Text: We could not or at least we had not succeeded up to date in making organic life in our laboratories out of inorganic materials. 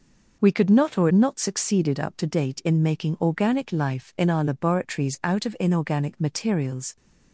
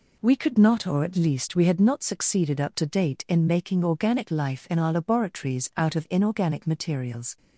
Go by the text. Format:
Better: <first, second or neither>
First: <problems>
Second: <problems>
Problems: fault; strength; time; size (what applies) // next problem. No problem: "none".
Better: second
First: skips "at least we had"; at 1.0 s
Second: none